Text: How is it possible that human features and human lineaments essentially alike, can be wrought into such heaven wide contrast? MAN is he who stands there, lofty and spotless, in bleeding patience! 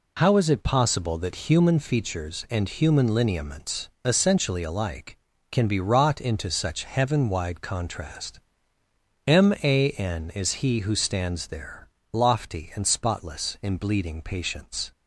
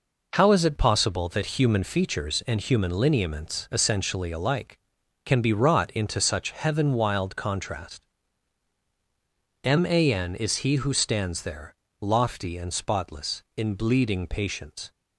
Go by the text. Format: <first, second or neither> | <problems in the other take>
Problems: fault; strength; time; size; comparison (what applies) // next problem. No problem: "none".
first | says "wild" for "wide"; at 6.9 s